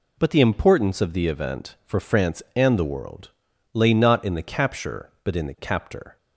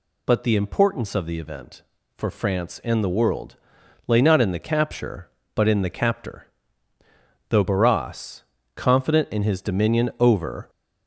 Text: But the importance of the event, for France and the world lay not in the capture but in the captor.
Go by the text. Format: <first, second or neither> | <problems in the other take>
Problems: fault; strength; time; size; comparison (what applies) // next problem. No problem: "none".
first | pauses between "world" and "lay"; noticeable; at 3.5 s; 0.50 s long; also in the first // goes on to say "Though Barras confident in his dominion over"; strong; from 7.4 s on; 3.2 s long